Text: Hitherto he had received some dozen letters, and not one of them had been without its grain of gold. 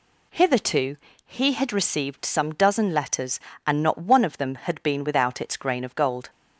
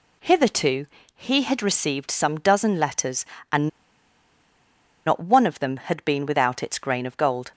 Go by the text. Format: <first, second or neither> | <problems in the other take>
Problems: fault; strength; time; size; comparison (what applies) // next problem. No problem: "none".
first | pauses between "Hitherto" and "he"; slight; at 0.8 s; 0.30 s long; slight in the first // pauses between "and" and "not"; strong; at 3.6 s; 1.3 s long